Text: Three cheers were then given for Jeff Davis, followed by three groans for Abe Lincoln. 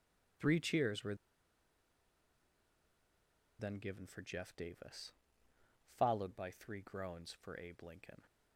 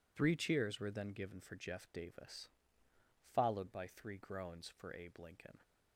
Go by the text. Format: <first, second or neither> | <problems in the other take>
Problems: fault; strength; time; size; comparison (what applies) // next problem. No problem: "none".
second | pauses between "were" and "then"; strong; at 1.1 s; 2.4 s long